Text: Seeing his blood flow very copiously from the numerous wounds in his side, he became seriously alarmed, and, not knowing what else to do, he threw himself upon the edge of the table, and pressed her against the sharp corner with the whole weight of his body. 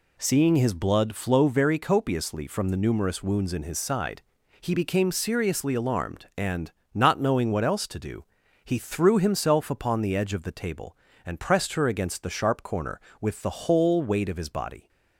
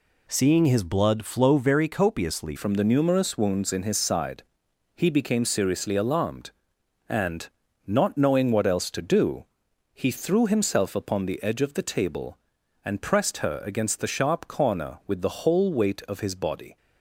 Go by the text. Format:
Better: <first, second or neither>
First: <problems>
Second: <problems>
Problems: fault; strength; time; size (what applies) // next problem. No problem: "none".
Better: first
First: none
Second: changes voice at "from"; from 2.5 s on; 14.2 s long